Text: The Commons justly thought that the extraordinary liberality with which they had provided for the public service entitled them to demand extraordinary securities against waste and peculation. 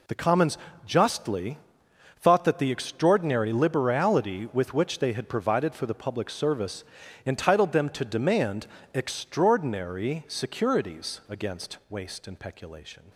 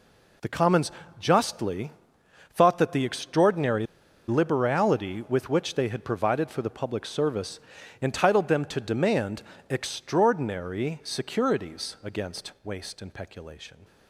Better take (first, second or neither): first